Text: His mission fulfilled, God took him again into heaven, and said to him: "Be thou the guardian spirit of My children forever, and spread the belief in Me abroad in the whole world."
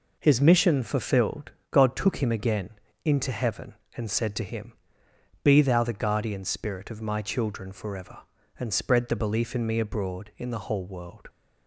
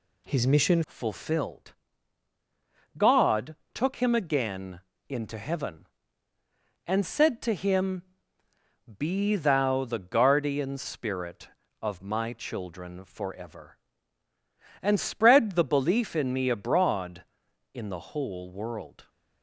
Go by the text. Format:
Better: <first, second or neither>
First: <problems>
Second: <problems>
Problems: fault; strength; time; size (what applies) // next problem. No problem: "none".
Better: first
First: pauses between "again" and "into"; slight; at 2.6 s; 0.34 s long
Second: changes voice at "fulfilled"; from 0.8 s on; 18.2 s long // pauses between "God" and "took"; slight; at 3.5 s; 0.18 s long // pauses between "again" and "into"; slight; at 4.7 s; 0.30 s long